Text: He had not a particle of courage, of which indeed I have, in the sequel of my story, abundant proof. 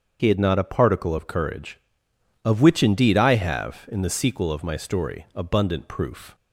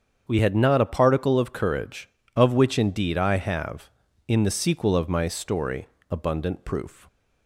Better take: first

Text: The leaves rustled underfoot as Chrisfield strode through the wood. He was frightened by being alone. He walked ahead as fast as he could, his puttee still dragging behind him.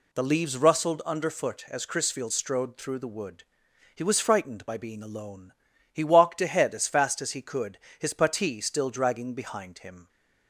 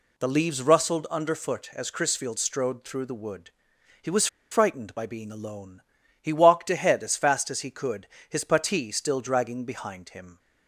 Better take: first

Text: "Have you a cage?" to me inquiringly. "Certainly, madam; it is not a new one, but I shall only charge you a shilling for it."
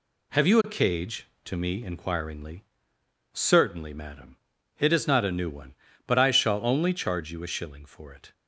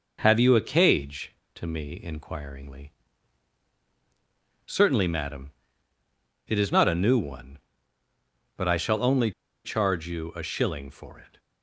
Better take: first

